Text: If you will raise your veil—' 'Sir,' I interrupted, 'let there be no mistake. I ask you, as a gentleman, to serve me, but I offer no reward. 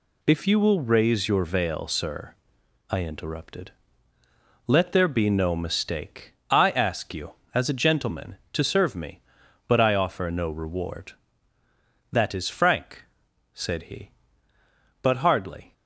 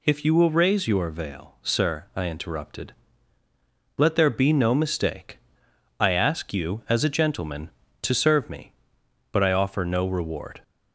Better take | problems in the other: second | goes on to say "That is frank said he but hardly"; strong; from 12.1 s on; 3.6 s long

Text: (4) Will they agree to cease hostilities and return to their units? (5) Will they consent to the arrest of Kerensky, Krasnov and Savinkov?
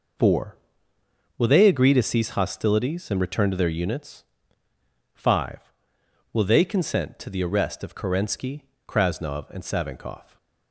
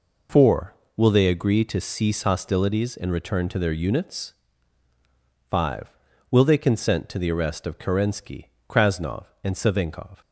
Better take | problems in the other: neither | none

